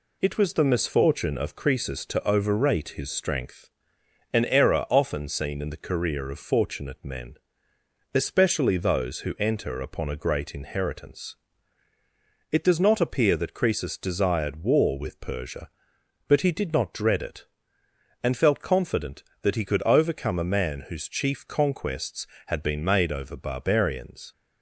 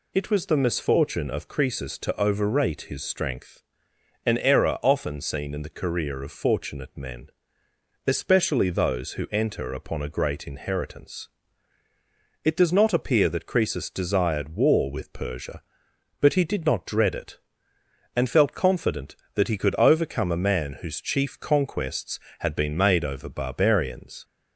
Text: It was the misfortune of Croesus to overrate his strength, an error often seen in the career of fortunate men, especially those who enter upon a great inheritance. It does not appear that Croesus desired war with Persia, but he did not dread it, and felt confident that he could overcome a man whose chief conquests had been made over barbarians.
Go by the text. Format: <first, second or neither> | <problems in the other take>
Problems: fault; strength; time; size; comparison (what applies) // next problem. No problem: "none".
second | gets quieter; slight; throughout; 2.5 dB